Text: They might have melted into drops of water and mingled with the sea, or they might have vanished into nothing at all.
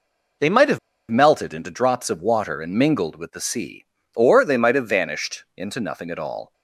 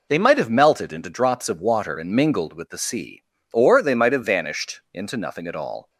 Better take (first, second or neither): second